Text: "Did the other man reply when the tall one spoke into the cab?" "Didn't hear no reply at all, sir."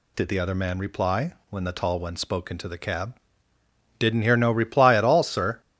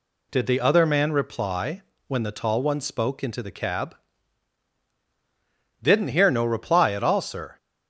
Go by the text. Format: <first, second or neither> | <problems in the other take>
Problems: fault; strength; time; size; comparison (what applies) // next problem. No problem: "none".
neither | pauses between "reply" and "when"; slight; the same in both